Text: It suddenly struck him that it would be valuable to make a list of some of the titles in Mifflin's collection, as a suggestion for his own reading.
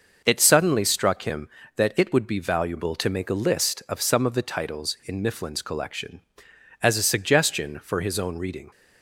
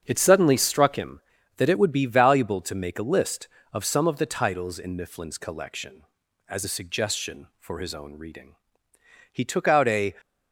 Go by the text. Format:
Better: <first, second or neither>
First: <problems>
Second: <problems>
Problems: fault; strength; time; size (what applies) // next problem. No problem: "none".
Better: first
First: none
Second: starts louder than the rest; strong; until 1.0 s; 7 dB // goes on to say "He took out a"; noticeable; from 9.3 s on; 0.82 s long